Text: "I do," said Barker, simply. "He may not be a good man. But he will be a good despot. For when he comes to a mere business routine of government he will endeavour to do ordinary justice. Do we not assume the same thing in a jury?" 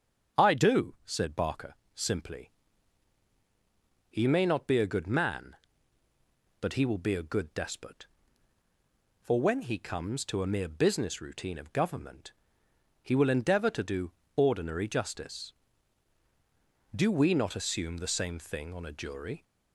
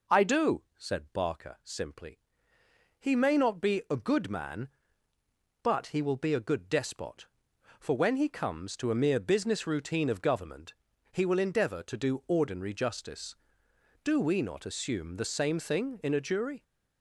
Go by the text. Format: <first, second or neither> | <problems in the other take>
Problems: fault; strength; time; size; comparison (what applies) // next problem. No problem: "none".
second | starts louder than the rest; strong; until 1.4 s; 8 dB // pauses between "government" and "he"; noticeable; at 12.3 s; 0.68 s long; also in the second // pauses between "do" and "ordinary"; slight; at 14.1 s; 0.24 s long // says "on" for "in"; at 18.7 s